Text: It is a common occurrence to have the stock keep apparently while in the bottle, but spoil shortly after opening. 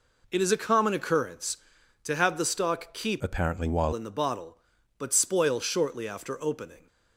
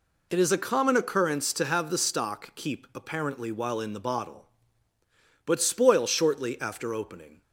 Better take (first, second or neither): second